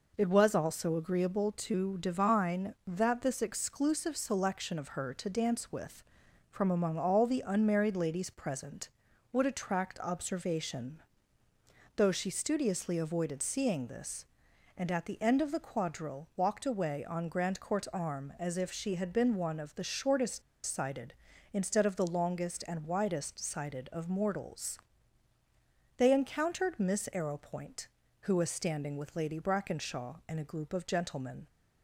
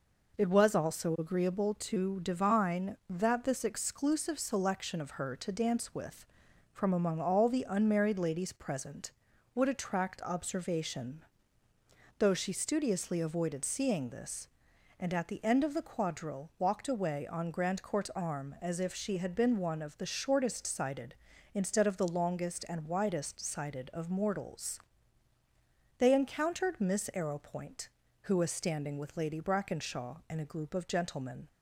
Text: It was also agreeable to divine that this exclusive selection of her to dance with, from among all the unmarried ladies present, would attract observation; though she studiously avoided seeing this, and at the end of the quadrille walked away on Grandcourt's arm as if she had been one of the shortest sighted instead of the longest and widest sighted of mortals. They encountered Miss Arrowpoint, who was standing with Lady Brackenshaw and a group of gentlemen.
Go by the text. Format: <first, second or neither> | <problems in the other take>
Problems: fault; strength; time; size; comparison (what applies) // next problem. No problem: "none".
second | pauses between "shortest" and "sighted"; slight; at 20.4 s; 0.24 s long